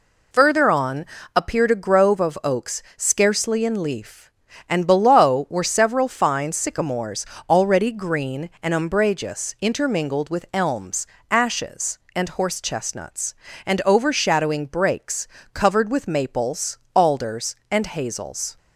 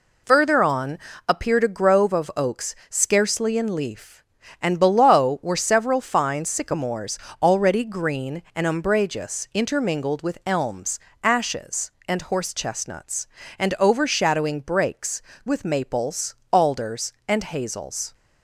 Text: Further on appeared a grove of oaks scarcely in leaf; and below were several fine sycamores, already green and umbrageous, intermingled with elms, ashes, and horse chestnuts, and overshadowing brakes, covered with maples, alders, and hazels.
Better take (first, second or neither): first